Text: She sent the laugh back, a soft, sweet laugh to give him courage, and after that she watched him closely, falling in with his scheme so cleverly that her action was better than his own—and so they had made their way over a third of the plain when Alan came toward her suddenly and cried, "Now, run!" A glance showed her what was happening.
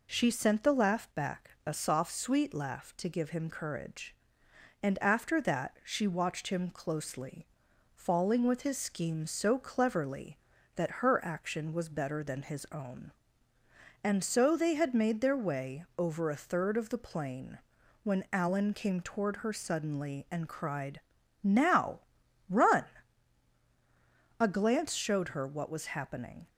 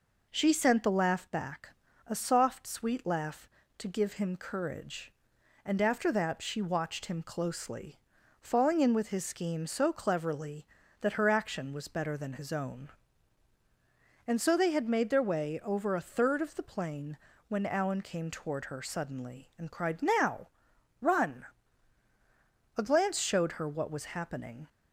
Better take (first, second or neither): second